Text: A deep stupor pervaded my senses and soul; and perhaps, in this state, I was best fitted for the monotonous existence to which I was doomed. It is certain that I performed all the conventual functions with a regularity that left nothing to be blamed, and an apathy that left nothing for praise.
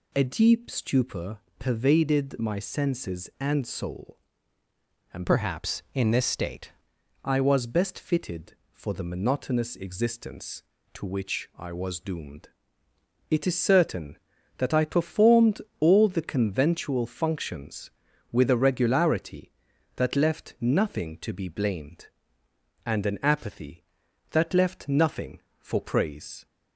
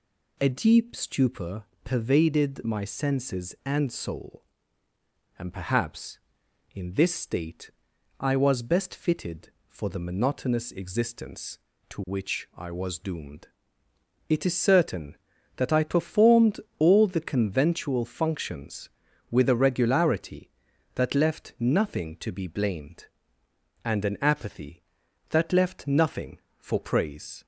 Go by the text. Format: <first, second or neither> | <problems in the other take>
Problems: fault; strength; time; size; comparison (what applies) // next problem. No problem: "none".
second | pauses between "stupor" and "pervaded"; slight; at 1.3 s; 0.20 s long; slight in the second // changes voice from "perhaps" to "state"; from 5.2 to 6.7 s; 1.5 s long // pauses between "performed" and "all"; slight; at 15.5 s; 0.20 s long; slight in the second